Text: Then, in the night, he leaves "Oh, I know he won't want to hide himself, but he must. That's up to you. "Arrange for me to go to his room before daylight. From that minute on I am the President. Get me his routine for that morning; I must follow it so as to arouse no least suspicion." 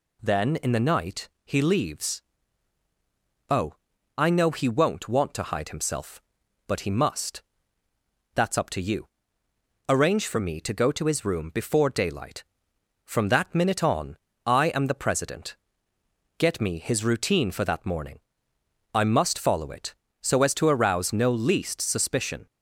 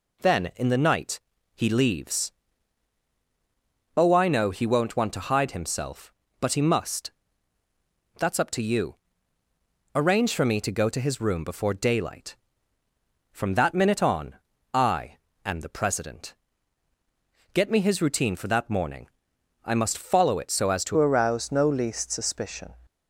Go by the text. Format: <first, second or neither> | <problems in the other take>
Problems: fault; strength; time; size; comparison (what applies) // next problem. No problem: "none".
first | pauses between "leaves" and "Oh"; strong; at 2.3 s; 1.6 s long; strong in the first // pauses between "on" and "I"; at 14.3 s; 0.38 s long; slight in the first // pauses between "I" and "am"; slight; at 15.1 s; 0.28 s long // changes voice at "arouse"; from 20.9 s on; 1.8 s long